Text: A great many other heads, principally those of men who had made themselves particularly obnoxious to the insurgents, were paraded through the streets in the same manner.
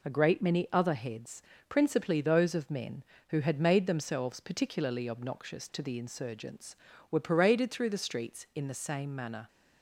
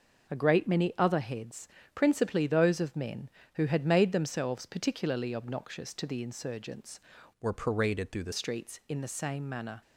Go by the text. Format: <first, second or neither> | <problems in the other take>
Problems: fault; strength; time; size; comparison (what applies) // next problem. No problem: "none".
first | changes voice from "were" to "the"; from 7.3 to 8.3 s; 1.0 s long